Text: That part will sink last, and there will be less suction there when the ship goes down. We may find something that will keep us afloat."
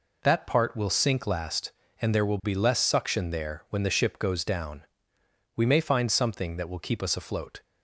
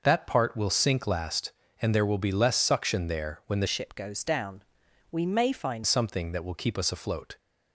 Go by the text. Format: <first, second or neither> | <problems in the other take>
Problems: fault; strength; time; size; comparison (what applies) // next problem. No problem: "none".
first | changes voice from "ship" to "find"; from 3.6 to 5.8 s; 2.2 s long